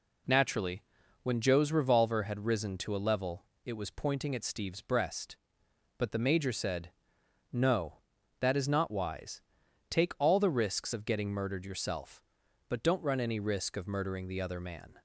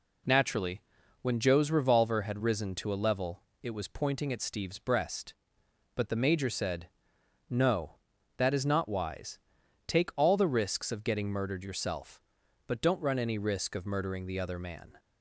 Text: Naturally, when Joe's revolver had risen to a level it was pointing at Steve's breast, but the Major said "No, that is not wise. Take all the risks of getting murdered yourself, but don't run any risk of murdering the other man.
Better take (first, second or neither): neither